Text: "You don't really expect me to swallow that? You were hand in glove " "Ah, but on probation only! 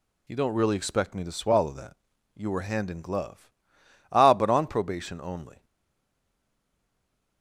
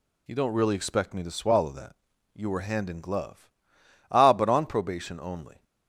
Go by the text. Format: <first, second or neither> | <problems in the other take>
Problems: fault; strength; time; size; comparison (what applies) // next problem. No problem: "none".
second | stays silent after the last word; noticeable; from 5.6 s on; 1.8 s long